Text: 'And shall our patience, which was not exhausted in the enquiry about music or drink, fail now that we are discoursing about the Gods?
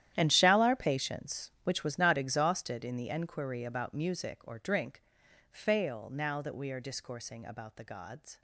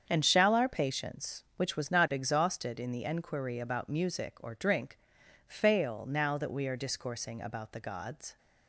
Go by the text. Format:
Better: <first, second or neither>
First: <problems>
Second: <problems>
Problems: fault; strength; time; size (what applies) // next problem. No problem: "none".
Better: second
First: gets quieter; strong; throughout; 16.5 dB // starts louder than the rest; strong; until 1.1 s; 11.5 dB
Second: starts louder than the rest; strong; until 1.0 s; 7.5 dB